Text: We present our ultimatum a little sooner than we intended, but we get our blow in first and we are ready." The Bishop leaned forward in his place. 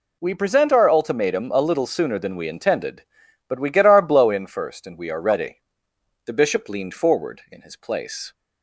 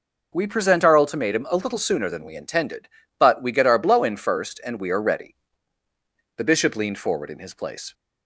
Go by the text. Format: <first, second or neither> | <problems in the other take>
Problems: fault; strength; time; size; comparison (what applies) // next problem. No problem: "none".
neither | none